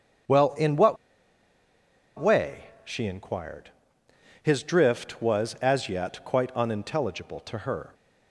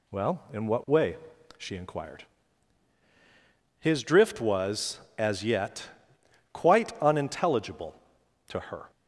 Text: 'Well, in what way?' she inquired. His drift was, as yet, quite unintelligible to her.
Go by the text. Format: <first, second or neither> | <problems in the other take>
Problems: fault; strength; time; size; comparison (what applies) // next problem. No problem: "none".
second | starts louder than the rest; strong; until 2.5 s; 7.5 dB // pauses between "what" and "way"; at 0.9 s; 1.2 s long